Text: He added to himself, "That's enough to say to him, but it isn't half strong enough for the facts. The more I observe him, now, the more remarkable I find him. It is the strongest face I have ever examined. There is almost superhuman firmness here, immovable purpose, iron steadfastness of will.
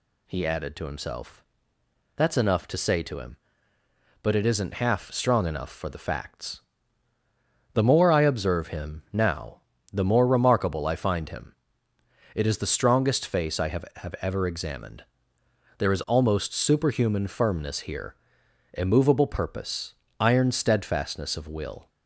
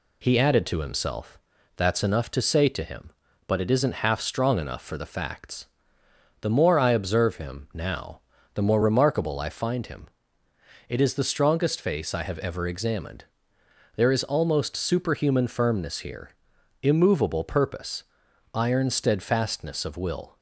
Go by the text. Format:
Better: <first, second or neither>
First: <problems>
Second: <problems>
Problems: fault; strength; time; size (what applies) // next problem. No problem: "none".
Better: second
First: says "have" twice; at 13.9 s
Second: none